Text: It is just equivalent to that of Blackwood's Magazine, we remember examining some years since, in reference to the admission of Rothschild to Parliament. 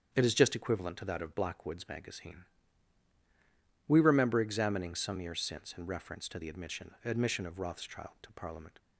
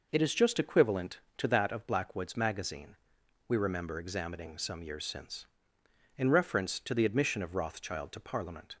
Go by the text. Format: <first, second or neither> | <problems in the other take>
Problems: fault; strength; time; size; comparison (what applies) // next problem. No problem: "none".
second | starts louder than the rest; strong; until 1.1 s; 7.5 dB // says "admission" twice; at 7.0 s